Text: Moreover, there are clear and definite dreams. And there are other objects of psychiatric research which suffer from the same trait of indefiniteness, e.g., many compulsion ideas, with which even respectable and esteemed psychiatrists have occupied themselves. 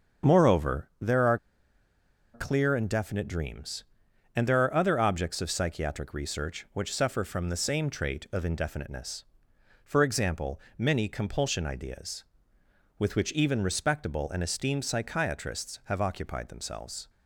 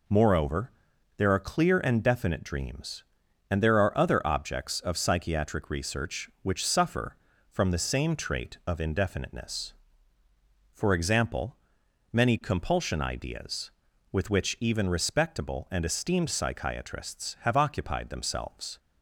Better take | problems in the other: second | starts louder than the rest; until 2.3 s; 7 dB // pauses between "are" and "clear"; noticeable; at 1.3 s; 0.97 s long

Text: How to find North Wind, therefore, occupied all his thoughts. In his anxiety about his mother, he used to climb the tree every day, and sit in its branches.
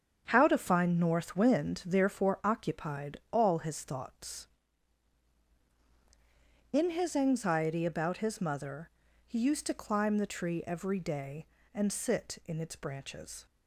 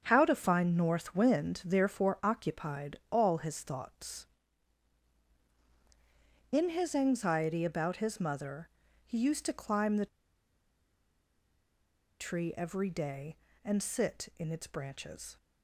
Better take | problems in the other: first | starts louder than the rest; strong; until 1.0 s; 7.5 dB; strong in the first // pauses between "the" and "tree"; strong; at 10.0 s; 2.1 s long

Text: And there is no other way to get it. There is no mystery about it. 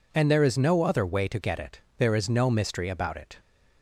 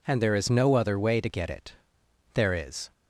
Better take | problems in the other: first | stops before "no mystery about it"; at 2.9 s

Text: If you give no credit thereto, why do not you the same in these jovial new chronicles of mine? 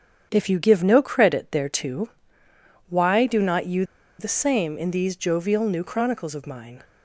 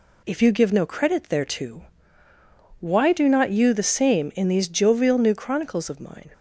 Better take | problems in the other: second | starts louder than the rest; strong; until 1.3 s; 7.5 dB // pauses between "you" and "the"; slight; at 3.8 s; 0.35 s long

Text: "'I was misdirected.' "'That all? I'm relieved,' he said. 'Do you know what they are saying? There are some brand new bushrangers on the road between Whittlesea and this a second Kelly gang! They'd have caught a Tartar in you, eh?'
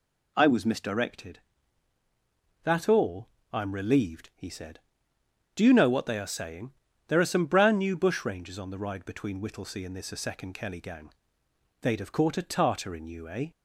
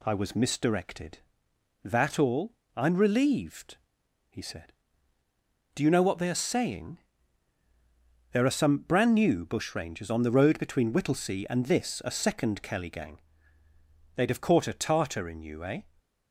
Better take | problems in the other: second | says "ride" for "road"; at 8.7 s

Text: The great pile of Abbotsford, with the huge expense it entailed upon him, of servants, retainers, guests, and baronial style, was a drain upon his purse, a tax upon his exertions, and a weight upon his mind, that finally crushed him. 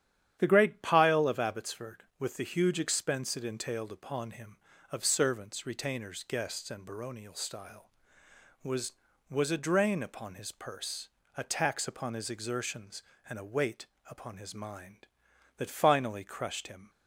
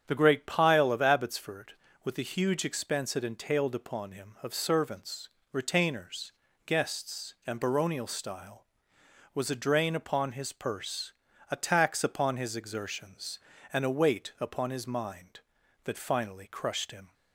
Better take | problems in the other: second | starts louder than the rest; strong; until 1.4 s; 10 dB; strong in the second // says "was" twice; at 9.2 s // pauses between "weight" and "upon"; slight; at 13.8 s; 0.24 s long

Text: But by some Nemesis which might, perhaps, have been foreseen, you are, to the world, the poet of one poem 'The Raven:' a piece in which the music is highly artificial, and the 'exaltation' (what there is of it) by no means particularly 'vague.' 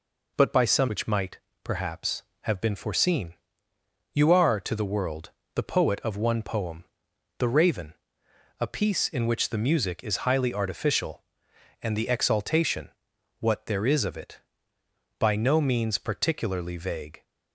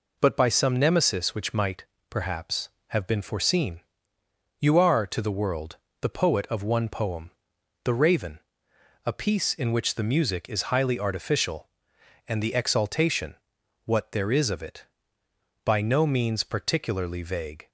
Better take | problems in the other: second | skips "Nemesis"; at 0.8 s // pauses between "poem" and "The"; noticeable; at 6.8 s; 0.54 s long; noticeable in the second

